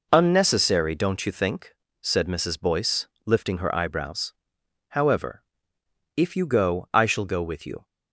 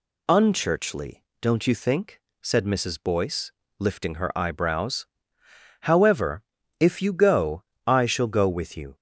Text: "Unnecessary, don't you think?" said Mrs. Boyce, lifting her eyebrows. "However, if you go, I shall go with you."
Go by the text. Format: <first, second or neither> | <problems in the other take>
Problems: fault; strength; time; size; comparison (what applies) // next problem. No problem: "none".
first | says "Unchurchly" for "Unnecessary"; at 0.2 s